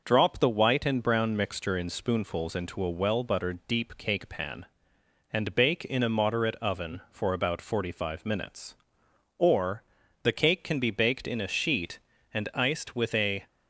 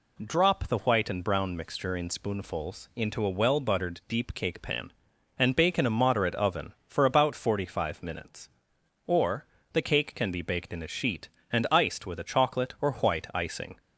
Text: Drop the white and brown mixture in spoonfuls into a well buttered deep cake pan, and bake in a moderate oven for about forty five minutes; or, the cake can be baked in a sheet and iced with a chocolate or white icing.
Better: second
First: stops before "chocolate or white icing"; at 13.4 s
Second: none

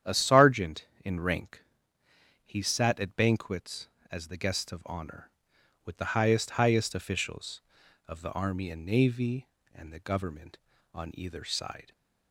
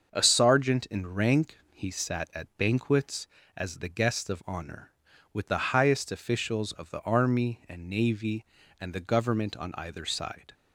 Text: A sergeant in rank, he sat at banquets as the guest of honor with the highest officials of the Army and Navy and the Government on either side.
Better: second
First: starts louder than the rest; strong; until 1.2 s; 9.5 dB // says "highest" twice; at 6.5 s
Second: starts louder than the rest; until 1.1 s; 6.5 dB

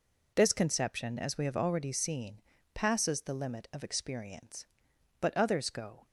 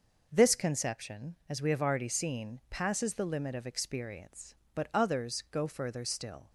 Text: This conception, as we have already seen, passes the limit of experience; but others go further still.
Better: second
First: stops before "further still"; at 6.0 s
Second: none

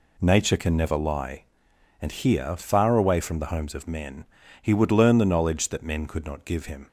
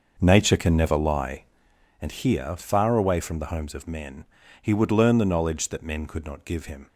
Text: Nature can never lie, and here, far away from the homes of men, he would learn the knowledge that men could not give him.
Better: first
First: none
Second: starts louder than the rest; noticeable; until 1.9 s; 6 dB

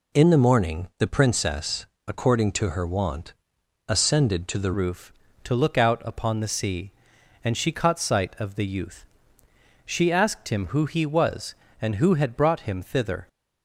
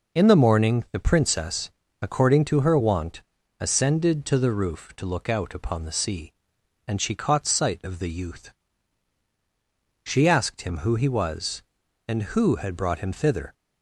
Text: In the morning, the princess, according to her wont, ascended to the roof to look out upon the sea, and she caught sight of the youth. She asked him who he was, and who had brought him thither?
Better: second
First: changes voice at "roof"; from 4.7 s on; 8.5 s long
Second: none

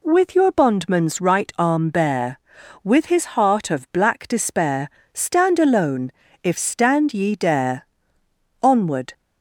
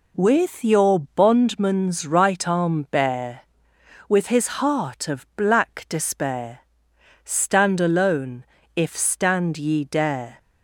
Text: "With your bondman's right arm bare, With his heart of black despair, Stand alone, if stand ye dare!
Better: second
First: goes on to say "Onward"; from 8.6 s on; 0.52 s long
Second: none

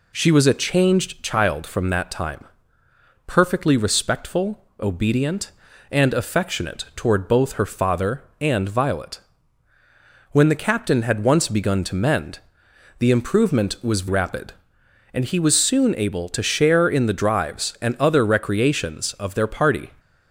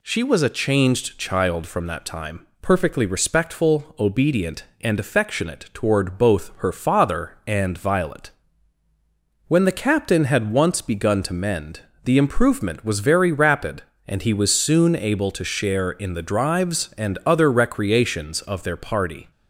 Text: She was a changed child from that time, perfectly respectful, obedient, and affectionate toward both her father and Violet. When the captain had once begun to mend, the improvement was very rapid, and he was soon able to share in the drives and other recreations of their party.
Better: second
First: skips "very"; at 14.0 s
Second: none

